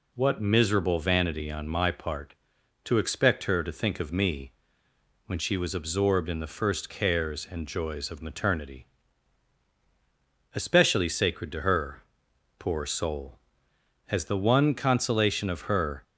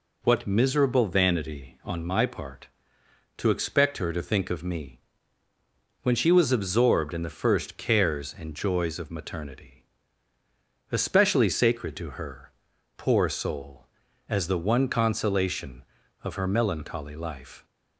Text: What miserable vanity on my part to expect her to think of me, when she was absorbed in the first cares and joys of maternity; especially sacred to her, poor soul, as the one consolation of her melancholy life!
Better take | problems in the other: second | stops before "melancholy life"; at 16.0 s

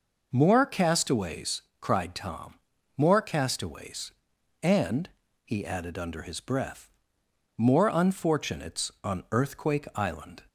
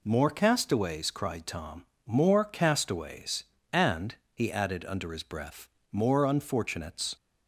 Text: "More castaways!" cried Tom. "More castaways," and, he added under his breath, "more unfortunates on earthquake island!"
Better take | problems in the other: first | stops before "on earthquake island"; at 7.1 s

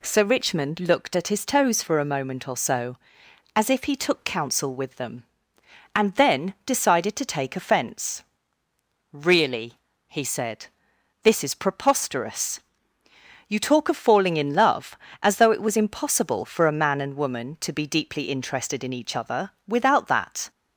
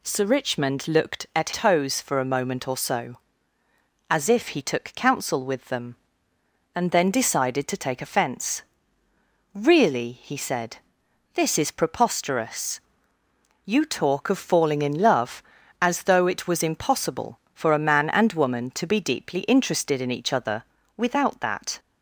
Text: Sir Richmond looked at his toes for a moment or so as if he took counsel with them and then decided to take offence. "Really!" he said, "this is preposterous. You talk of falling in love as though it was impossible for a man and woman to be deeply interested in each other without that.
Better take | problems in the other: first | skips "his"; at 1.5 s // pauses between "other" and "without"; slight; at 20.6 s; 0.32 s long; slight in the first

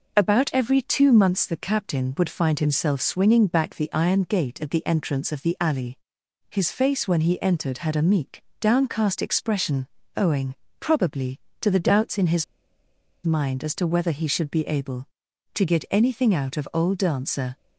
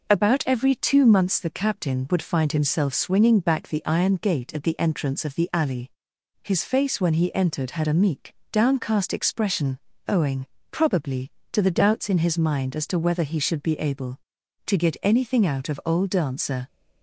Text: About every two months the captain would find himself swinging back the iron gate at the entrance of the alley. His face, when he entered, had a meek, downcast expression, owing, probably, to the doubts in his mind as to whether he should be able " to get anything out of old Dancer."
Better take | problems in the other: second | pauses between "his" and "mind"; noticeable; at 12.4 s; 0.80 s long

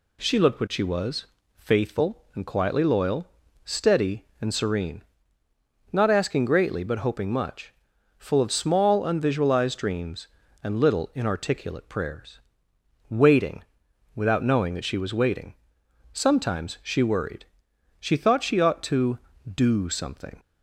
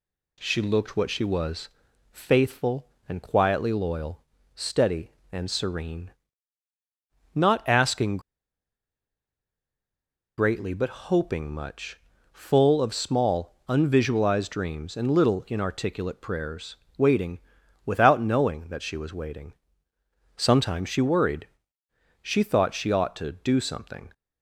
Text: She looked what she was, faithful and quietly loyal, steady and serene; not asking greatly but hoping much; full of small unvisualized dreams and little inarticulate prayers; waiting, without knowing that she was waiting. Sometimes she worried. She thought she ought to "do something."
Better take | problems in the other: first | pauses between "asking" and "greatly"; strong; at 8.1 s; 2.1 s long

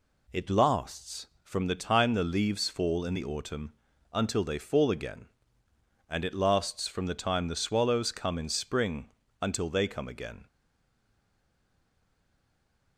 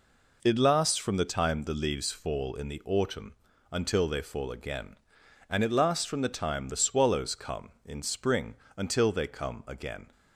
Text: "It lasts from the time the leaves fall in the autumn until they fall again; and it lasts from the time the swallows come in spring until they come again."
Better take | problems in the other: second | pauses between "autumn" and "until"; at 3.7 s; 0.40 s long; also in the second // pauses between "spring" and "until"; slight; at 9.0 s; 0.32 s long; slight in the second // stays silent after the last word; from 10.4 s on; 2.5 s long

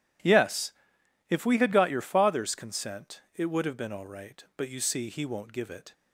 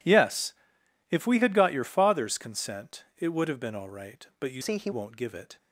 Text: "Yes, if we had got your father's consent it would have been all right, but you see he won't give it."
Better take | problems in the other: first | pauses between "consent" and "it"; slight; at 3.0 s; 0.16 s long; slight in the first // changes voice from "see" to "he"; from 4.6 to 4.9 s; 0.3 s long

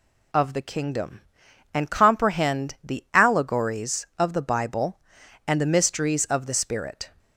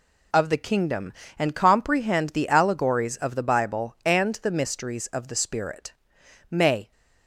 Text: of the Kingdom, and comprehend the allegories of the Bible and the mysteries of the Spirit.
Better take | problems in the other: first | goes on to say "May"; slight; from 6.4 s on; 0.42 s long

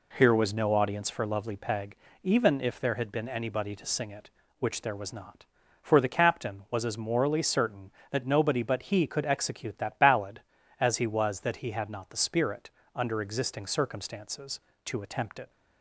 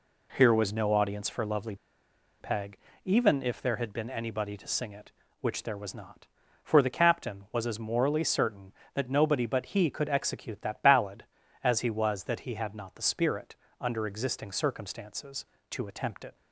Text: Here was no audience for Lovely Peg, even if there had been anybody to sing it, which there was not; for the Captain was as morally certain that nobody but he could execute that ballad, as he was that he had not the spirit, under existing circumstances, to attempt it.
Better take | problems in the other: first | pauses between "Lovely" and "Peg"; noticeable; at 1.7 s; 0.65 s long

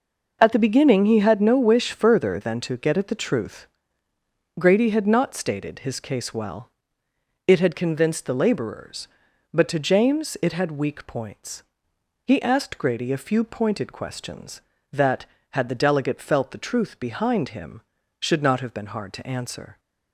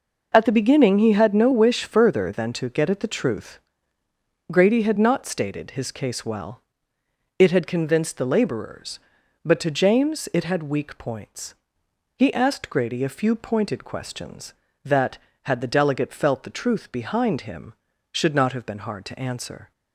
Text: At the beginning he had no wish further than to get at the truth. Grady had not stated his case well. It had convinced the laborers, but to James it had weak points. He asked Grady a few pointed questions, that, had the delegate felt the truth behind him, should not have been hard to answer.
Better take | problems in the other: neither | none

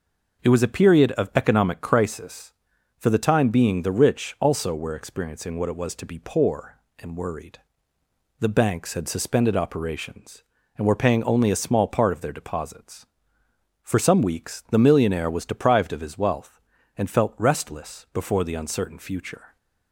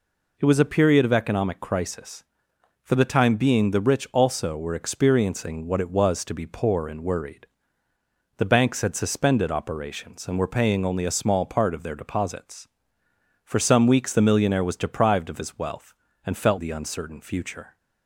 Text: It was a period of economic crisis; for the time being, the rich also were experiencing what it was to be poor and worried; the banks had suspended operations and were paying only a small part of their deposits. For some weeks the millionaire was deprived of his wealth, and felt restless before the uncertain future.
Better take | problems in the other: first | skips "restless before"; at 16.5 s

